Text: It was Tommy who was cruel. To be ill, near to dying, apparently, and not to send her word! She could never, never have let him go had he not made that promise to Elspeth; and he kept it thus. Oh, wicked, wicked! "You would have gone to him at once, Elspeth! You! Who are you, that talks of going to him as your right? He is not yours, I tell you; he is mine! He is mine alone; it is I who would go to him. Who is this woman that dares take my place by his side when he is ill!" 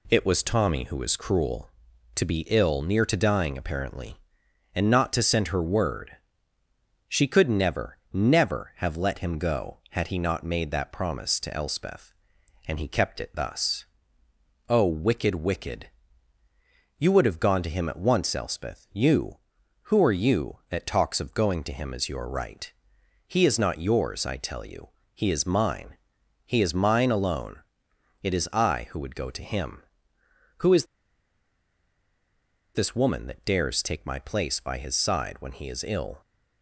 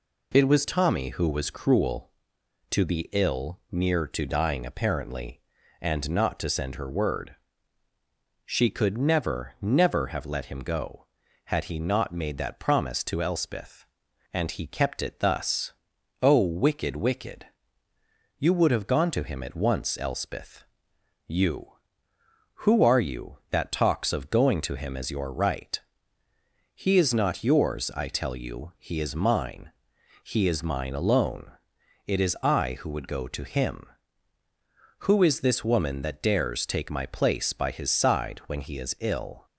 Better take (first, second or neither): second